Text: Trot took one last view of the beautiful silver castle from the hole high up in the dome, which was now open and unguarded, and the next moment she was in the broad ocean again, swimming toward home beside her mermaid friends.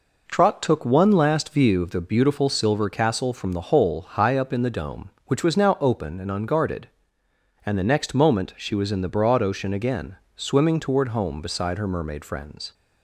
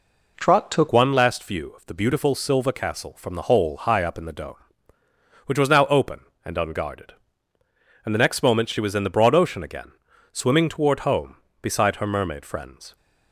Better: first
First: none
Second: changes voice at "one"; from 0.9 s on; 12.0 s long

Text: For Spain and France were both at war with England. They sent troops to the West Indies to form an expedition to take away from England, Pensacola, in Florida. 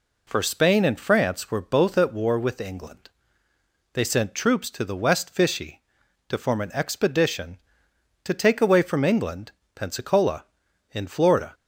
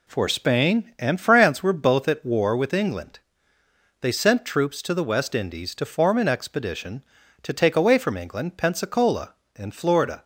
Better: second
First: says "Fishy" for "Indies"; at 5.2 s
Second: none

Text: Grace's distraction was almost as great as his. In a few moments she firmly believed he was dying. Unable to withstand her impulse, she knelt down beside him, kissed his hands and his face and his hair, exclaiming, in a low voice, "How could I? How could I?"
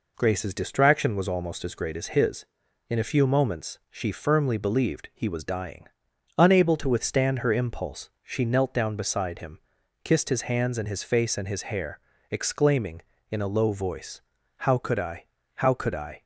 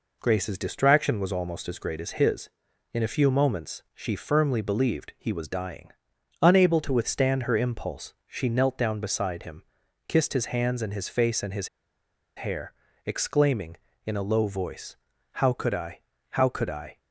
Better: first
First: none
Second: pauses between "his" and "hair"; noticeable; at 11.6 s; 0.69 s long

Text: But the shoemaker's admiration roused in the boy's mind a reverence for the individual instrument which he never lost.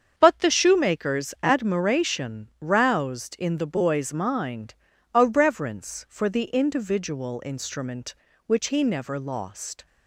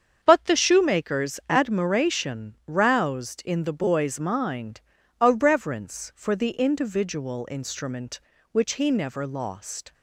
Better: neither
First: starts louder than the rest; strong; until 1.1 s; 7.5 dB // pauses between "mind" and "a"; at 4.7 s; 0.40 s long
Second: starts louder than the rest; strong; until 1.2 s; 7.5 dB // pauses between "mind" and "a"; at 4.7 s; 0.40 s long

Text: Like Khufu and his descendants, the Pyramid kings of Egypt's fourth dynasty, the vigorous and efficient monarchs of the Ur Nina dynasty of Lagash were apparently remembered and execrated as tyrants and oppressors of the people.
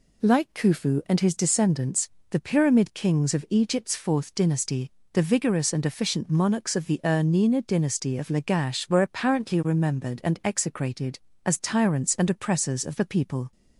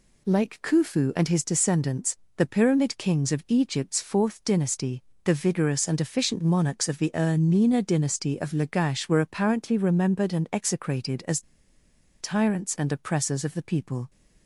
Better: first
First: none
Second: pauses between "as" and "tyrants"; noticeable; at 11.4 s; 0.79 s long

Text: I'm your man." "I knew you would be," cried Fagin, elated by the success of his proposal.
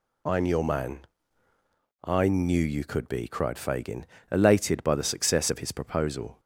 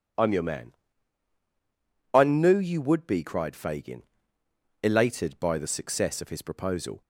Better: second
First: says "could" for "would"; at 2.8 s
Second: none

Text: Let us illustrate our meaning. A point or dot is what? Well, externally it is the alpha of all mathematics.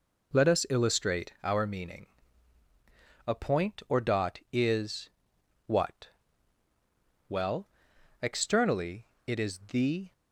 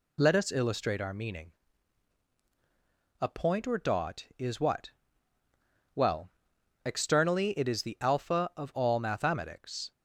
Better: second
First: pauses between "is" and "what"; noticeable; at 5.0 s; 0.56 s long // pauses between "externally" and "it"; slight; at 9.0 s; 0.20 s long // stops before "alpha of all mathematics"; at 10.1 s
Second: none

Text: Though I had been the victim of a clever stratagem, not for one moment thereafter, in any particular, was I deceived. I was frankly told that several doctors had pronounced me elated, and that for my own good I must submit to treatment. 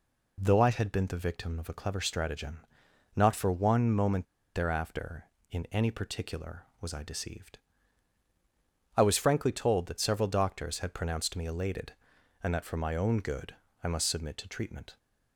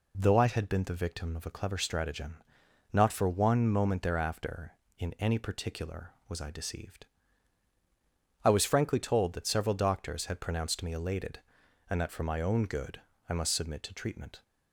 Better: second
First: pauses between "moment" and "thereafter"; slight; at 4.2 s; 0.29 s long // pauses between "good" and "I"; slight; at 13.5 s; 0.28 s long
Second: pauses between "good" and "I"; slight; at 12.9 s; 0.28 s long

